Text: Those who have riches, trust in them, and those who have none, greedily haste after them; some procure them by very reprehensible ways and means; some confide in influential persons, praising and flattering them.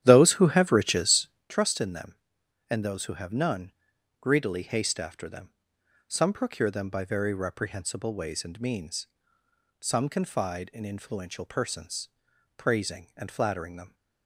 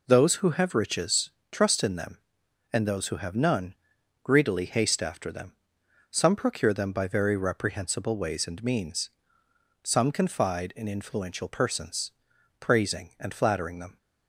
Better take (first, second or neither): second